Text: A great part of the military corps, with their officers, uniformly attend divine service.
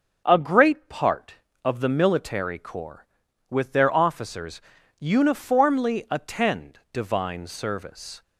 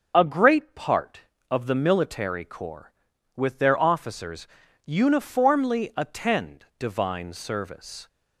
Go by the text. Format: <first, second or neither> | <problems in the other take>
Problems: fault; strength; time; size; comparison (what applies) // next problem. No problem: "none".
first | loses the start of "A"; at 0.1 s; 35 ms // starts louder than the rest; until 1.1 s; 6.5 dB; also in the first // pauses between "attend" and "divine"; slight; at 6.6 s; 0.16 s long; slight in the first